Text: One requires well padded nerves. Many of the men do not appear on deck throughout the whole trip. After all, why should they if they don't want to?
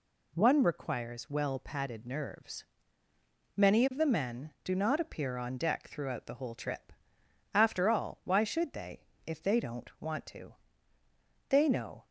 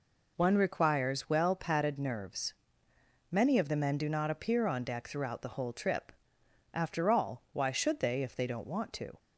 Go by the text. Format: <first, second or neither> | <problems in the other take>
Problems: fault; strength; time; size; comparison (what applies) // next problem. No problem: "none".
second | pauses between "they" and "if"; slight; at 9.0 s; 0.20 s long // goes on to say "They know"; from 11.4 s on; 0.58 s long